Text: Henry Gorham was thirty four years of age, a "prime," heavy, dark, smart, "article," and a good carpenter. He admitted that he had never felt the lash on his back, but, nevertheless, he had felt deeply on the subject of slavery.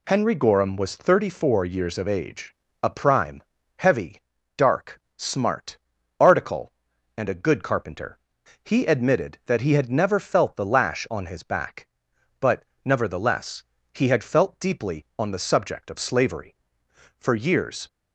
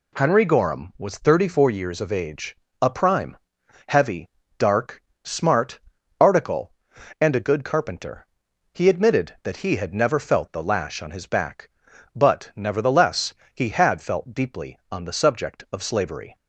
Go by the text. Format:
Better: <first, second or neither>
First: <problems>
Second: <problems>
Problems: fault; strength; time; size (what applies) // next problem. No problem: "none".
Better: second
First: goes on to say "For years"; noticeable; from 17.1 s on; 0.70 s long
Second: none